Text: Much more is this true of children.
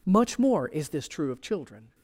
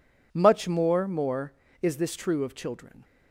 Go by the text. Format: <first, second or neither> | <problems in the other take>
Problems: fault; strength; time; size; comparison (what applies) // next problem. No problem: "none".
first | says "more" twice; at 1.0 s